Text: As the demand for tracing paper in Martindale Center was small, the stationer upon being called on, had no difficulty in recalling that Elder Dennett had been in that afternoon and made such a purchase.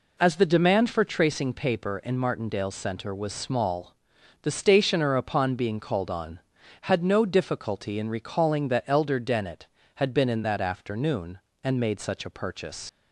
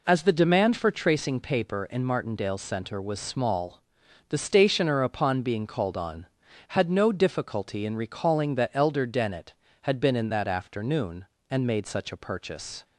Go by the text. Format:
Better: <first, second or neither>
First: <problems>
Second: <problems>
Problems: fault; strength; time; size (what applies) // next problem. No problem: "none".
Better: second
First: leaves "purchase" unfinished; at 12.8 s; 80 ms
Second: none